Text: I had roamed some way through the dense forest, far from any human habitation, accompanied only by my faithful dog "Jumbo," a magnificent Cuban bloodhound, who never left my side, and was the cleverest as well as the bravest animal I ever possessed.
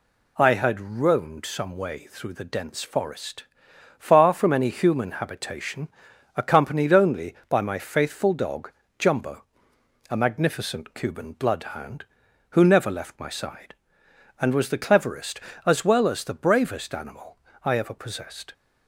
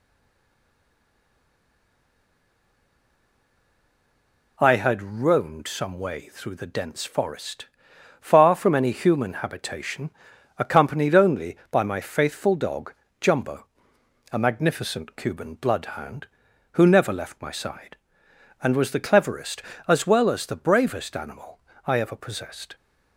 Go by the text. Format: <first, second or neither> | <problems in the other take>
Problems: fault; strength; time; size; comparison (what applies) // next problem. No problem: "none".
first | stays silent before the first word; strong; until 4.5 s; 4.5 s long // pauses between "dog" and "Jumbo"; slight; at 12.9 s; 0.26 s long; slight in the first // pauses between "animal" and "I"; slight; at 21.5 s; 0.28 s long; slight in the first